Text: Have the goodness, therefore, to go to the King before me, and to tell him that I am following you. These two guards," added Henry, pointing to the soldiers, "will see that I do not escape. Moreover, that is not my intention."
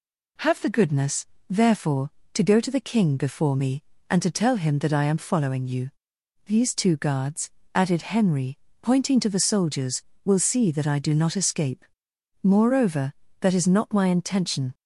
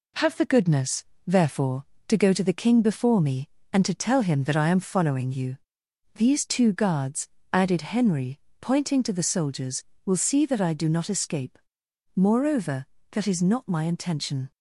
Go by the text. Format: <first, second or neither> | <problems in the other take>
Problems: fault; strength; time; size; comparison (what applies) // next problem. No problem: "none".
first | gets quieter; noticeable; throughout; 4 dB